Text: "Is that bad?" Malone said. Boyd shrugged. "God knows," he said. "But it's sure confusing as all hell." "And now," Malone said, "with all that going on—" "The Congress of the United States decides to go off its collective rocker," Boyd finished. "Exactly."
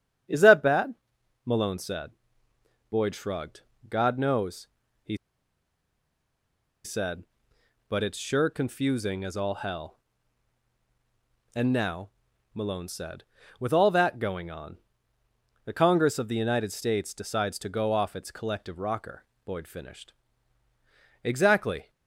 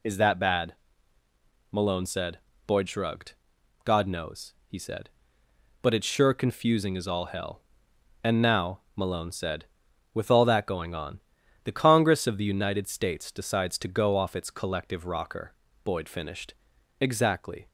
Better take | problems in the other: second | starts louder than the rest; strong; until 1.8 s; 8.5 dB // pauses between "he" and "said"; strong; at 5.1 s; 1.6 s long

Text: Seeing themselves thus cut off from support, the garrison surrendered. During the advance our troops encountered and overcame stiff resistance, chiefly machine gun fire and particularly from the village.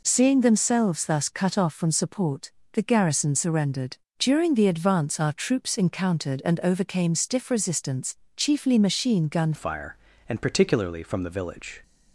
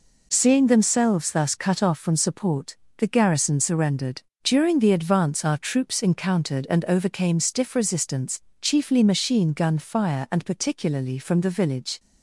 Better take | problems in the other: second | changes voice at "fire"; from 9.5 s on; 2.3 s long

